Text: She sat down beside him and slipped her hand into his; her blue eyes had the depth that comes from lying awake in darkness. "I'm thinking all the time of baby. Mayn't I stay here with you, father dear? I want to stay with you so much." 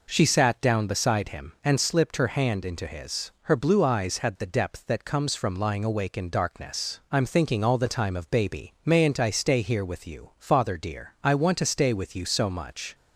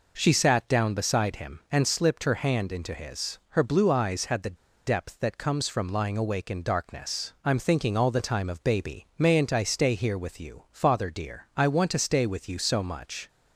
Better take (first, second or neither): first